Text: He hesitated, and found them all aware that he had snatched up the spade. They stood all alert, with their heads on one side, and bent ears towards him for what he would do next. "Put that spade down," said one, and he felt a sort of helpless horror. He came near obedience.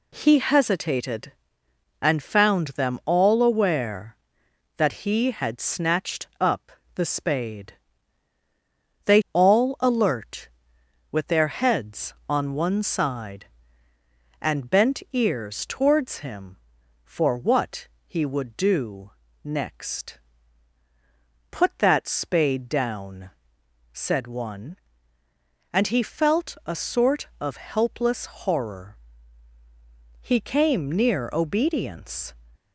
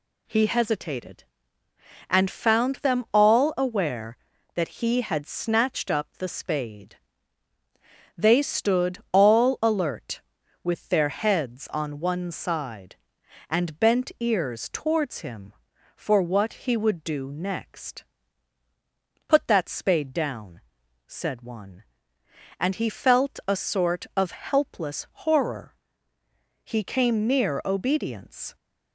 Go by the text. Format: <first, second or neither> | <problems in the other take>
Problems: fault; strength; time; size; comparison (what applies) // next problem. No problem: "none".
second | pauses between "up" and "the"; slight; at 6.6 s; 0.24 s long // skips "stood"; at 9.2 s // pauses between "what" and "he"; slight; at 17.8 s; 0.18 s long // pauses between "do" and "next"; slight; at 19.1 s; 0.32 s long // pauses between "helpless" and "horror"; slight; at 28.2 s; 0.20 s long